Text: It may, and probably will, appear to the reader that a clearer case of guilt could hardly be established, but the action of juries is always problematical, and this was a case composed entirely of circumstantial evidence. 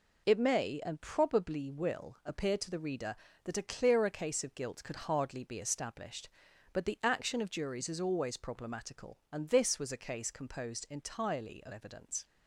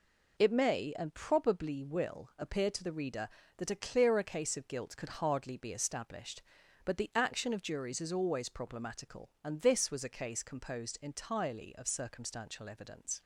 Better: second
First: skips "circumstantial"; at 11.7 s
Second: none

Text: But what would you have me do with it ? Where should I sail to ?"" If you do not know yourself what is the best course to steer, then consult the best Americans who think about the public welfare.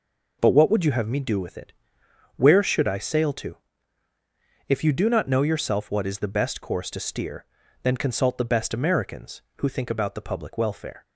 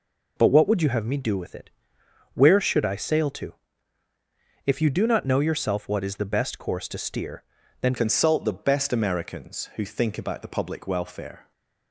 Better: first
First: none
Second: changes voice at "consult"; from 7.9 s on; 3.6 s long

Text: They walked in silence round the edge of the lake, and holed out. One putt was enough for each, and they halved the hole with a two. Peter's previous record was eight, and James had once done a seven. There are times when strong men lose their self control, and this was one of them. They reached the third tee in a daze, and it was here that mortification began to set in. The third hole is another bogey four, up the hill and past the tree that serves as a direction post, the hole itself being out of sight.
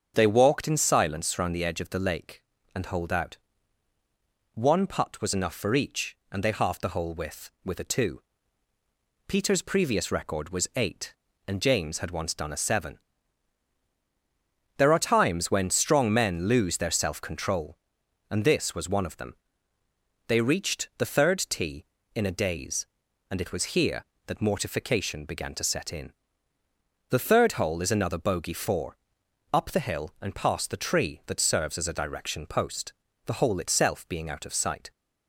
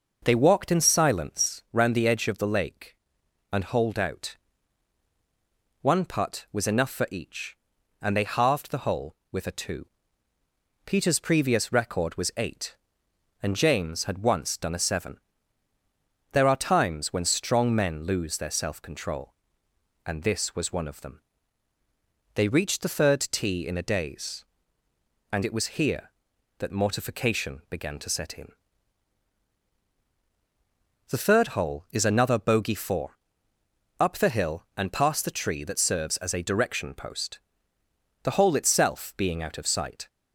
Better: second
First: starts louder than the rest; until 1.1 s; 7 dB // says "with" twice; at 7.6 s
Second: none

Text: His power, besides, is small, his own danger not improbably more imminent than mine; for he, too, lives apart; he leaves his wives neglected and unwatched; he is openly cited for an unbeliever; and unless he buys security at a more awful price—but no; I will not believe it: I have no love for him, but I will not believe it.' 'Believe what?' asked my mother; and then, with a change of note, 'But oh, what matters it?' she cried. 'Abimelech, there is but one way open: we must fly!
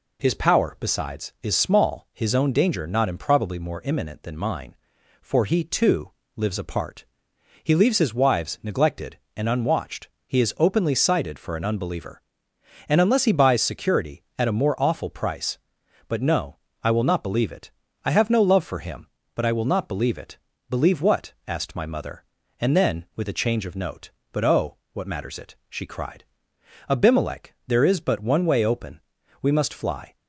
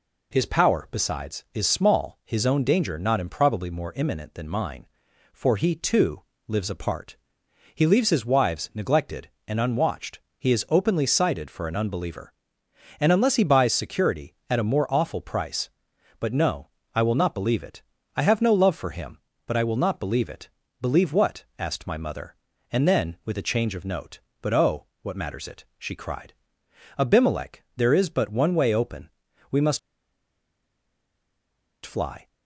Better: first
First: none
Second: pauses between "must" and "fly"; strong; at 29.7 s; 2.0 s long

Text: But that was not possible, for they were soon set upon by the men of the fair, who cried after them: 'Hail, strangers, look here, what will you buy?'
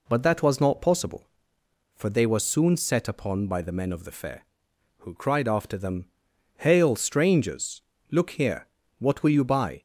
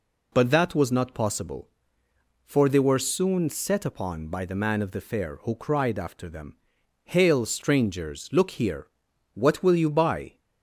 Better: first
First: none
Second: says "man" for "men"; at 4.5 s

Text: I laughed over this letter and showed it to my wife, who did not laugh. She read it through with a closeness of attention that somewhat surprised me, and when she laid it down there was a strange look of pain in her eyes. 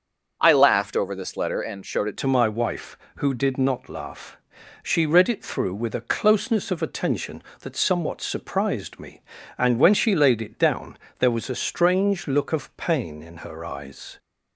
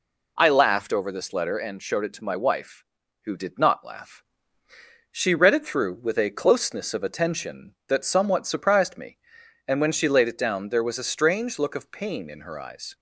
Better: second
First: starts louder than the rest; until 1.4 s; 6.5 dB // changes voice at "to"; from 2.1 s on; 12.0 s long // pauses between "down" and "there"; slight; at 10.9 s; 0.22 s long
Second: none

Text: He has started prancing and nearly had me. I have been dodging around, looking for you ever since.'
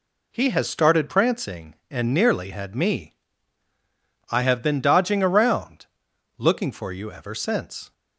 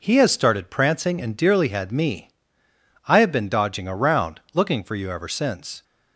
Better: first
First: none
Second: says "dearly" for "nearly"; at 1.3 s

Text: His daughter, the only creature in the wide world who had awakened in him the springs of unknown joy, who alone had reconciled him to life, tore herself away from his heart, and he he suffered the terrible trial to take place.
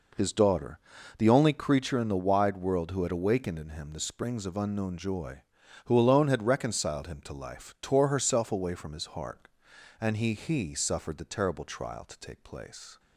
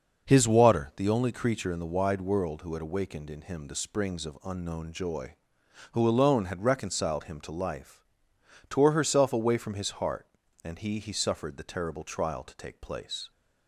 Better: first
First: none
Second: says "water" for "daughter"; at 0.4 s

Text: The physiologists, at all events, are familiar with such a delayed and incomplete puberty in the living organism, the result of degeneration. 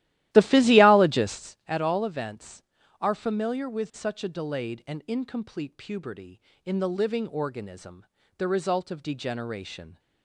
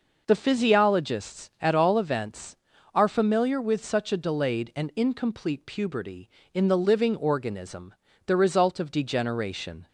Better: second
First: starts louder than the rest; strong; until 1.6 s; 15 dB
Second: none

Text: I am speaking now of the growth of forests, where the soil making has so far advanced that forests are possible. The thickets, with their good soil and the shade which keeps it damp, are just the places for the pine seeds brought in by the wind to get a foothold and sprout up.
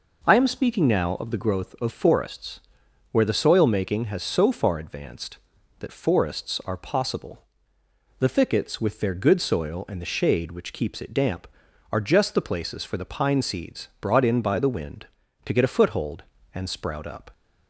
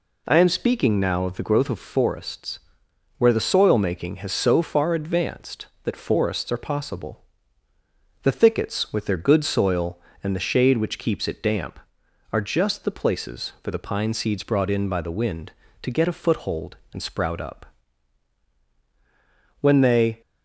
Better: first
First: none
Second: goes on to say "When they"; from 19.6 s on; 0.60 s long

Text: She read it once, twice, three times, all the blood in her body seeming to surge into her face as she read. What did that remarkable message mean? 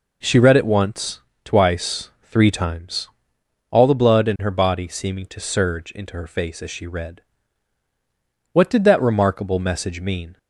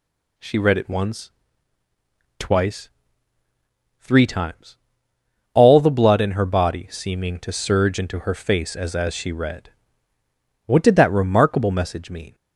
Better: first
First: none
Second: says "as" twice; at 8.9 s

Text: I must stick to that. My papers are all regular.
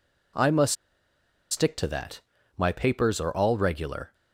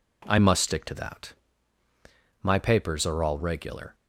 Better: second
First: pauses between "must" and "stick"; noticeable; at 0.7 s; 0.75 s long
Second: none

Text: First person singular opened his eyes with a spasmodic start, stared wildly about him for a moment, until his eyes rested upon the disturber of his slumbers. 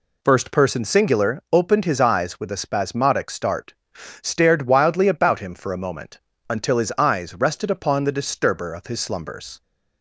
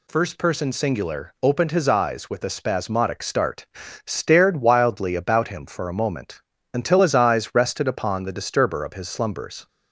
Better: neither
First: none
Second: none

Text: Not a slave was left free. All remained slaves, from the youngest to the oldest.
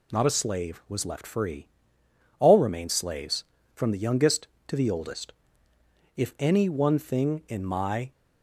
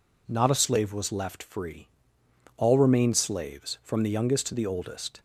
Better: second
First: goes on to say "If any one thing in my"; strong; from 6.1 s on; 1.9 s long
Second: none

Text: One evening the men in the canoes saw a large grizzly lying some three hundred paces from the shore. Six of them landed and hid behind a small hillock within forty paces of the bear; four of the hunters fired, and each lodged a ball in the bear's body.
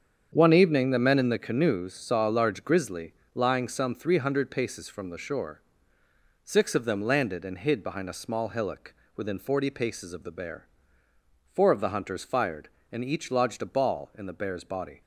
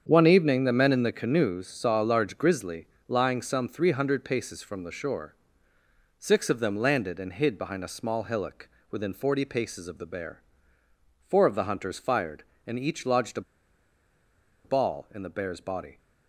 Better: first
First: starts louder than the rest; strong; until 1.3 s; 7.5 dB // pauses between "grizzly" and "lying"; slight; at 3.1 s; 0.22 s long // pauses between "hillock" and "within"; slight; at 8.9 s; 0.20 s long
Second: starts louder than the rest; strong; until 1.0 s; 7.5 dB // pauses between "grizzly" and "lying"; slight; at 2.8 s; 0.22 s long // pauses between "hillock" and "within"; slight; at 8.6 s; 0.20 s long // pauses between "a" and "ball"; at 13.4 s; 1.2 s long

